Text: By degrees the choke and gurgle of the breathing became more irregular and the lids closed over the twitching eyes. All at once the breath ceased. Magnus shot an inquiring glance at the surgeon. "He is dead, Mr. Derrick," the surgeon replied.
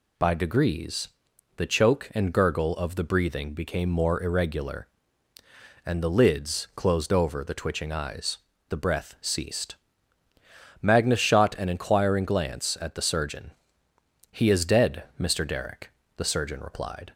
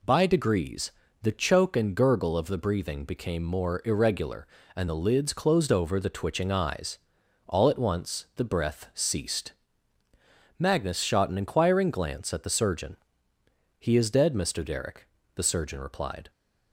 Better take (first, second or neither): second